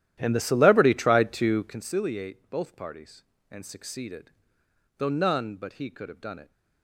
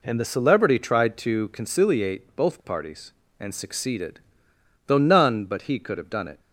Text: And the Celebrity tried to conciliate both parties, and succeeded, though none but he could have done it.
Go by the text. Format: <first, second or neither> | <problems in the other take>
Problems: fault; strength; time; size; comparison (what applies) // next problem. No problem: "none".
second | starts louder than the rest; strong; until 1.9 s; 12 dB